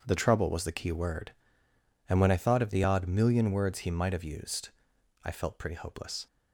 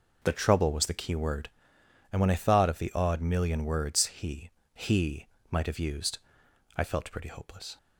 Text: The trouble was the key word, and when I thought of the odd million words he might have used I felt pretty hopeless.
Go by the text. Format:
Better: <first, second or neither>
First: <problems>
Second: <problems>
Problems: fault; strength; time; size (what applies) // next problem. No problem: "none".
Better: first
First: pauses between "used" and "I"; noticeable; at 4.7 s; 0.52 s long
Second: says "he" twice; at 4.7 s // pauses between "used" and "I"; noticeable; at 6.1 s; 0.58 s long